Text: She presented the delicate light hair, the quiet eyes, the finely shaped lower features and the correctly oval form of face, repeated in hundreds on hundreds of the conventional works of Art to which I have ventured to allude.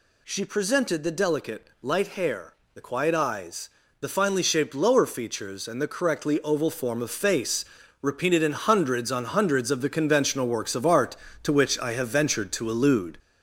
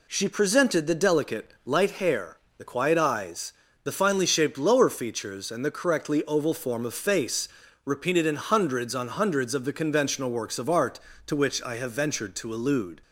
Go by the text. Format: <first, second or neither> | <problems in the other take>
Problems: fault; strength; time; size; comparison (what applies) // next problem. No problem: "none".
second | gets louder; noticeable; throughout; 4.5 dB // pauses between "delicate" and "light"; slight; at 1.6 s; 0.16 s long; slight in the second